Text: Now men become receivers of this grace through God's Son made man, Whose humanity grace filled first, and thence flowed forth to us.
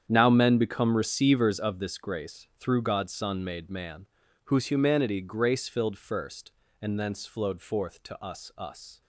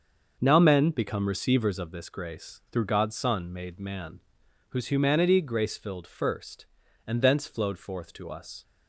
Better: second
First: starts louder than the rest; strong; until 1.0 s; 8.5 dB // says "us" twice; at 8.5 s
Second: starts louder than the rest; until 1.4 s; 6 dB

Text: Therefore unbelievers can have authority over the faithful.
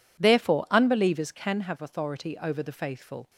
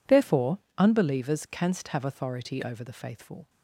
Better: first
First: none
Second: pauses between "Therefore" and "unbelievers"; slight; at 0.5 s; 0.20 s long // says "canst" for "can"; at 1.5 s

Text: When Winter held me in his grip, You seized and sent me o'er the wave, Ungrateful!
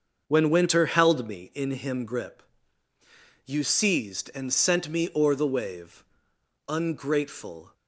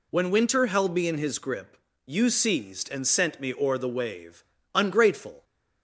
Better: second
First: starts louder than the rest; until 1.2 s; 6.5 dB // says "him" for "his"; at 1.6 s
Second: none

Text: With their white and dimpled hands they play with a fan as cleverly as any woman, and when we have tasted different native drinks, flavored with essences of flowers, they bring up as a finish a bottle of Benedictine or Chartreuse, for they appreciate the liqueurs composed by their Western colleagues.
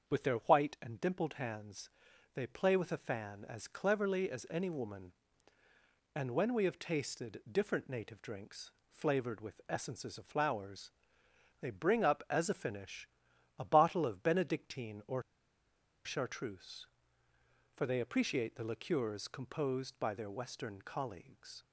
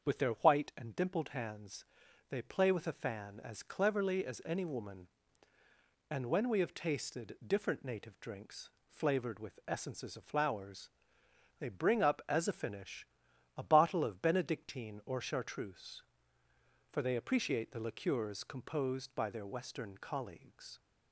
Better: second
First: starts louder than the rest; until 1.1 s; 7 dB // pauses between "hands" and "they"; noticeable; at 1.8 s; 0.46 s long // pauses between "finish" and "a"; noticeable; at 13.0 s; 0.50 s long // pauses between "or" and "Chartreuse"; noticeable; at 15.2 s; 0.82 s long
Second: starts louder than the rest; until 1.0 s; 7 dB // pauses between "hands" and "they"; noticeable; at 1.8 s; 0.46 s long // pauses between "finish" and "a"; noticeable; at 13.0 s; 0.50 s long

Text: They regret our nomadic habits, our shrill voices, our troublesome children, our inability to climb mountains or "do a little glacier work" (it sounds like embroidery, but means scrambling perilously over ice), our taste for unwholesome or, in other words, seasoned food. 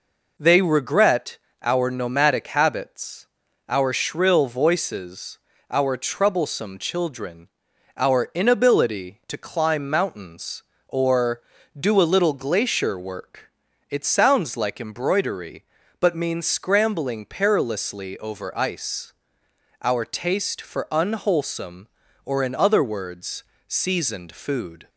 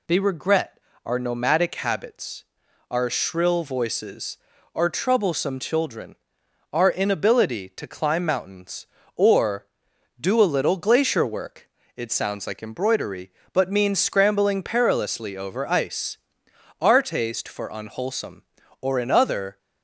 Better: first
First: pauses between "regret" and "our"; slight; at 1.3 s; 0.26 s long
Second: pauses between "regret" and "our"; slight; at 0.7 s; 0.26 s long // stops before "words seasoned food"; at 19.5 s

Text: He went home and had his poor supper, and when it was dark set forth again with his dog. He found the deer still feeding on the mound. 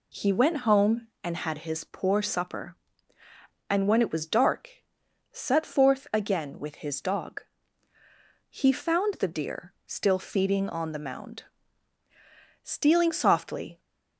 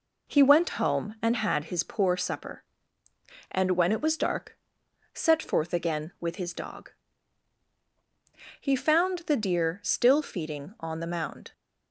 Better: second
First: pauses between "dark" and "set"; noticeable; at 4.8 s; 0.48 s long // pauses between "deer" and "still"; slight; at 9.7 s; 0.16 s long // goes on to say "Stealing softly"; noticeable; from 12.6 s on; 1.1 s long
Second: pauses between "dark" and "set"; noticeable; at 4.5 s; 0.56 s long

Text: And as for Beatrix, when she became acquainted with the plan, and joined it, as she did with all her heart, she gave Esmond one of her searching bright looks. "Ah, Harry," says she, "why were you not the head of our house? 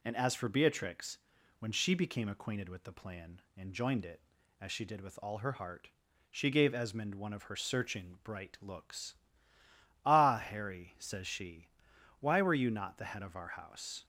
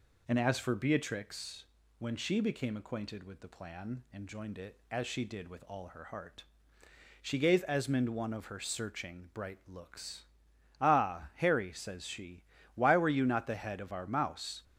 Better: first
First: none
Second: says "mouse" for "house"; at 14.0 s

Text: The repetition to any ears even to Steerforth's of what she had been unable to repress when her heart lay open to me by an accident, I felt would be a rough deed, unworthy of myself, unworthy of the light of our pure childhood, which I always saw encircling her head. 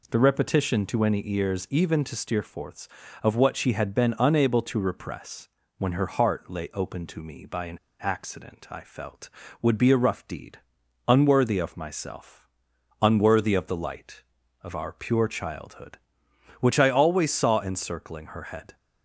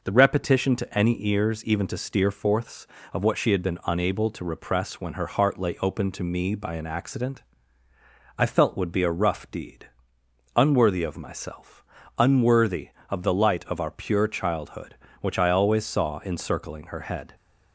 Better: second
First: pauses between "repress" and "when"; slight; at 5.4 s; 0.30 s long // pauses between "an" and "accident"; slight; at 7.7 s; 0.23 s long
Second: none

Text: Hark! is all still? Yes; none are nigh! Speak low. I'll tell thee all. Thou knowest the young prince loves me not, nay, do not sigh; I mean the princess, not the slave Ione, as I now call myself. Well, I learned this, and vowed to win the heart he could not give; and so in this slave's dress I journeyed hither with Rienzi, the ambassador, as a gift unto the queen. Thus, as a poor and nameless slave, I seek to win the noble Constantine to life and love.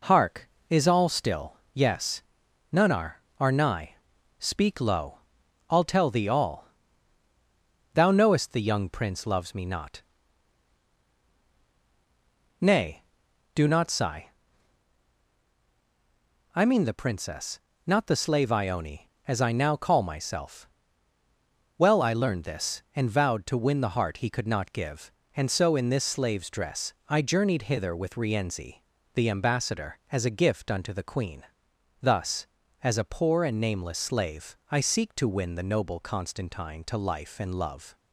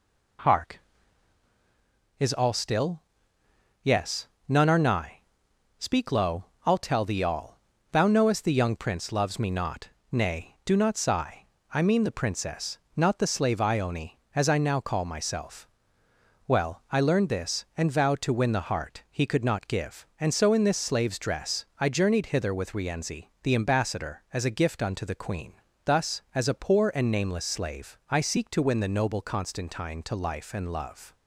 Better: second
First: says "are" twice; at 3.3 s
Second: none

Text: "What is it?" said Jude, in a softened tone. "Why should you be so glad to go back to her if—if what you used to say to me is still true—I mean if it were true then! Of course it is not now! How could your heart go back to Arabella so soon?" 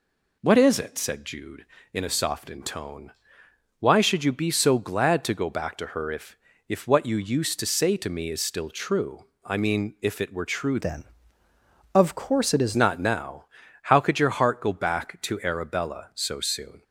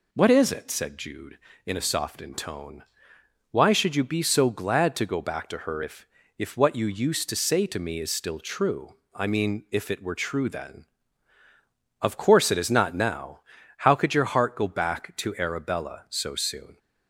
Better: second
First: changes voice from "then" to "is"; from 10.7 to 12.7 s; 2.0 s long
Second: none

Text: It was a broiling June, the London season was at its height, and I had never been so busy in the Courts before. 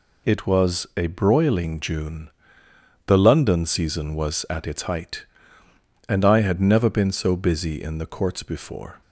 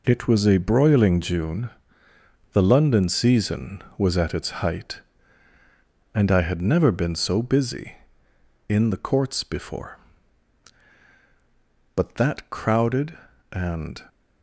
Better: first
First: none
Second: goes on to say "But that crowded and"; strong; from 11.9 s on; 2.0 s long

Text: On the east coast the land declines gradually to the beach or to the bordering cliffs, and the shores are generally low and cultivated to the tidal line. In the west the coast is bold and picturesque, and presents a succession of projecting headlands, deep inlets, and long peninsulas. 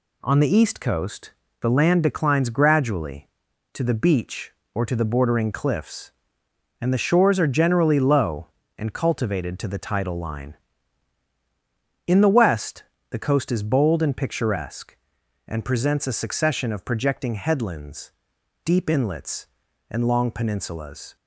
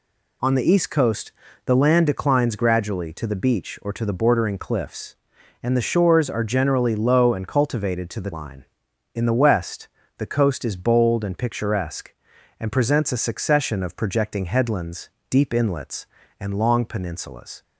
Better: first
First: pauses between "coast" and "the"; slight; at 1.3 s; 0.30 s long // pauses between "west" and "the"; slight; at 12.8 s; 0.28 s long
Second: pauses between "coast" and "the"; slight; at 1.3 s; 0.34 s long // skips "tidal"; at 8.3 s // pauses between "west" and "the"; slight; at 9.8 s; 0.28 s long

